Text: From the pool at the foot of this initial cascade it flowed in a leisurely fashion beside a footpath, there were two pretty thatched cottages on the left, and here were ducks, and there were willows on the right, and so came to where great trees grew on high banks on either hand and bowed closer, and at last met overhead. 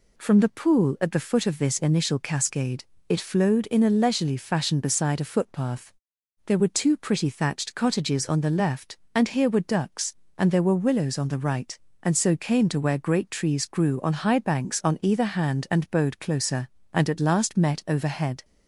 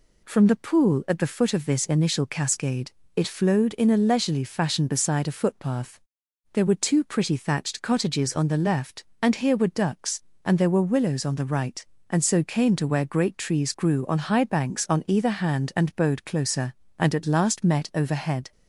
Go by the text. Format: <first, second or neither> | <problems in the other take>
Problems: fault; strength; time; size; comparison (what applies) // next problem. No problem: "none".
neither | pauses between "cascade" and "it"; slight; the same in both